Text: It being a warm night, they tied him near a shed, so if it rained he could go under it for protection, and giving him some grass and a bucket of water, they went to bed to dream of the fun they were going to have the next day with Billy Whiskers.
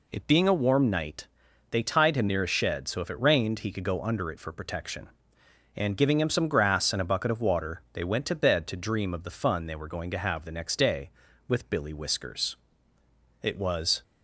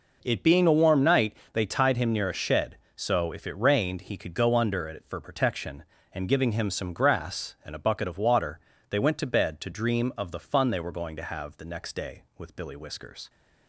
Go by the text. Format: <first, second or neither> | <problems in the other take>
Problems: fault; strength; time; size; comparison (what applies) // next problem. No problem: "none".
second | goes on to say "It was"; from 13.4 s on; 0.60 s long